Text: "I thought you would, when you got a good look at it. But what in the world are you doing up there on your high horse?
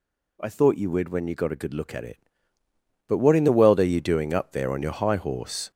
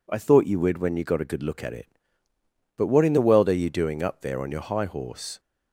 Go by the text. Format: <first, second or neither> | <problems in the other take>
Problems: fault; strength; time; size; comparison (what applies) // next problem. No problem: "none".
second | gets louder; noticeable; throughout; 4.5 dB